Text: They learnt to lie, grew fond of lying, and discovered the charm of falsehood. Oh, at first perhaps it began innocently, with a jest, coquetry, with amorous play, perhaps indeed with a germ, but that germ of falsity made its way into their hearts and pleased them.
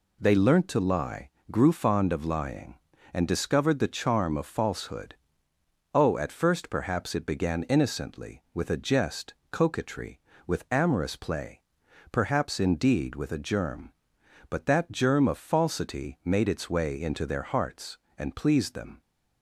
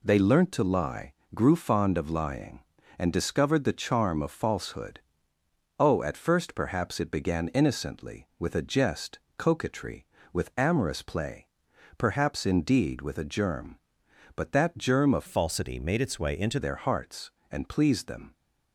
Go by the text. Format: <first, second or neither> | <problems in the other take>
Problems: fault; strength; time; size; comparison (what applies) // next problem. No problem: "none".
first | changes voice from "falsity" to "into"; from 15.2 to 16.5 s; 1.3 s long